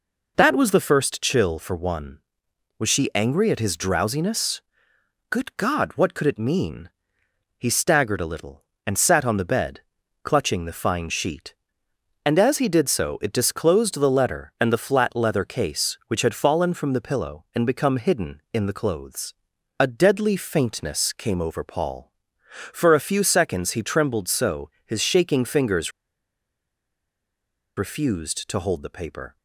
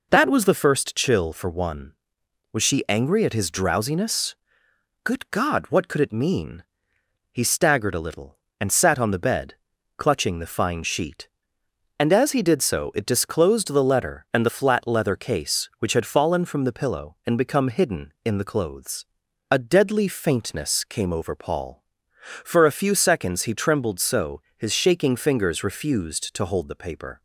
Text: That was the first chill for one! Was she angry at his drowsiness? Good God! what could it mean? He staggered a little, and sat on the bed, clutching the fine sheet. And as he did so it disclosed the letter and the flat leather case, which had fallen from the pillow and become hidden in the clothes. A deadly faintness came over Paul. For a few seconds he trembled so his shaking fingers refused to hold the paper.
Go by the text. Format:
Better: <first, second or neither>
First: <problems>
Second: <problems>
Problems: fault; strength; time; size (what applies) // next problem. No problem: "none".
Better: second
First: pauses between "so" and "his"; slight; at 24.6 s; 0.16 s long // pauses between "fingers" and "refused"; strong; at 25.9 s; 1.8 s long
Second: pauses between "so" and "his"; slight; at 24.4 s; 0.16 s long